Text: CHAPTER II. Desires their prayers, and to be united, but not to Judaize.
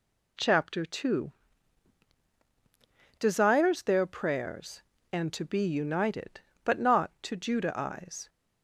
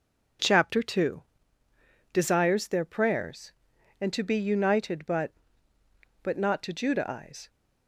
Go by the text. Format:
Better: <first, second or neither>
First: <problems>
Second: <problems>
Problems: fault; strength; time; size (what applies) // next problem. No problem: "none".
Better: first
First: none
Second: says "but" twice; at 6.2 s